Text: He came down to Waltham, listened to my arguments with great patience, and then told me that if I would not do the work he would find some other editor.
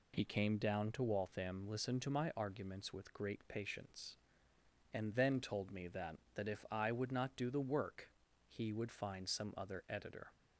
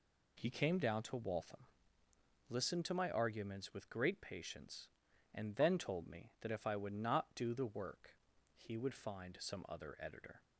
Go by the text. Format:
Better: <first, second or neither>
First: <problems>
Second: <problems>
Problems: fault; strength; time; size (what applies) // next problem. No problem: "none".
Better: second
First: says "that" twice; at 6.3 s // pauses between "work" and "he"; at 8.0 s; 0.38 s long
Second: pauses between "work" and "he"; at 8.1 s; 0.40 s long